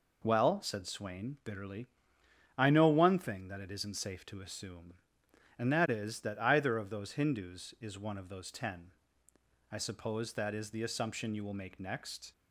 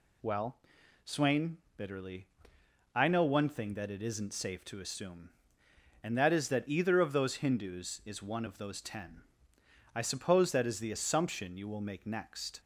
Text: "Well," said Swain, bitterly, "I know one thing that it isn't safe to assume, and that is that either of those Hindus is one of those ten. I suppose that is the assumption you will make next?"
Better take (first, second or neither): first